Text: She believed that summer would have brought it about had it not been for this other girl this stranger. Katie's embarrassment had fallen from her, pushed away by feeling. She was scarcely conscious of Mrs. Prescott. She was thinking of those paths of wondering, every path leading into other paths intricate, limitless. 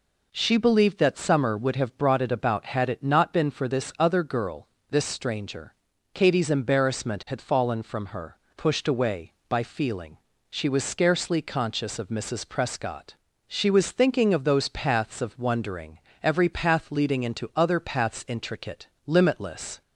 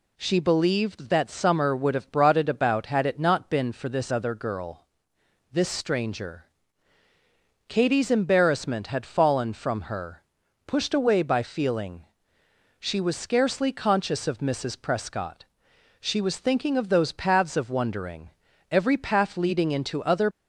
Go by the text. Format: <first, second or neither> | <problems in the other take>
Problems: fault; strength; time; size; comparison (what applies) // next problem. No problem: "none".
first | pauses between "girl" and "this"; noticeable; at 4.8 s; 0.68 s long; slight in the first // stops before "paths intricate limitless"; at 20.3 s